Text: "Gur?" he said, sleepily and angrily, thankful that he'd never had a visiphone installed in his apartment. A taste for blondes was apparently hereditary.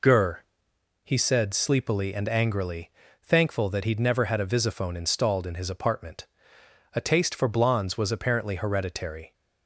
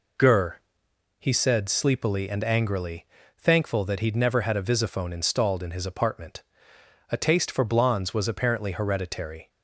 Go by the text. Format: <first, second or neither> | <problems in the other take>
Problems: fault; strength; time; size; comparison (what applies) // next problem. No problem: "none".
neither | none